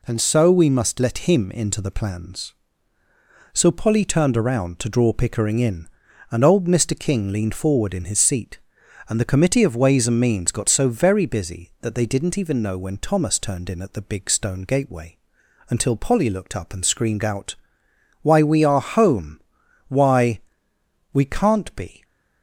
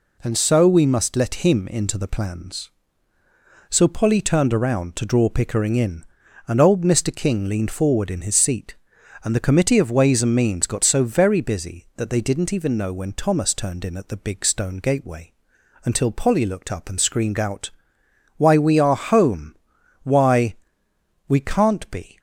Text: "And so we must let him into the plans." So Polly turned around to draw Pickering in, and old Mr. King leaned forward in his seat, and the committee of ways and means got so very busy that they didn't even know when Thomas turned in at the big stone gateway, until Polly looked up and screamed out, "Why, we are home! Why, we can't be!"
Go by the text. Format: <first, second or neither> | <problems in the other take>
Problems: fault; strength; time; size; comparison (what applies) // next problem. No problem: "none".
neither | none